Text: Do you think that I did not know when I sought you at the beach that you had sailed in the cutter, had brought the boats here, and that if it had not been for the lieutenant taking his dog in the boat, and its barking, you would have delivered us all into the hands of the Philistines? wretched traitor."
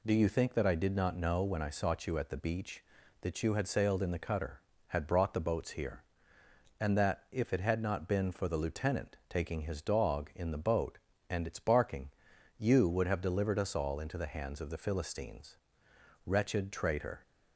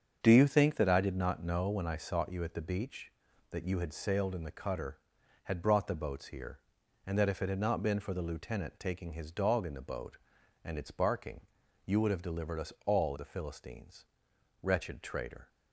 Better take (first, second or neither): first